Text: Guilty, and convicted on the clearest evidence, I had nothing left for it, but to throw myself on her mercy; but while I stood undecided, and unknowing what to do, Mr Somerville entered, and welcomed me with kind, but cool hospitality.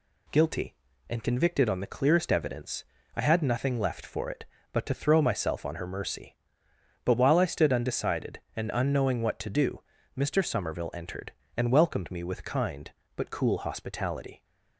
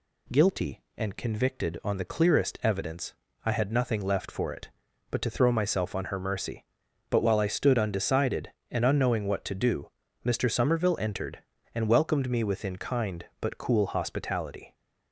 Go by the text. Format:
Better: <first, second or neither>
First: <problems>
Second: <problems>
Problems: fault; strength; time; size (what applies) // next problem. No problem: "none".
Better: first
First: none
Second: says "within" for "with"; at 12.4 s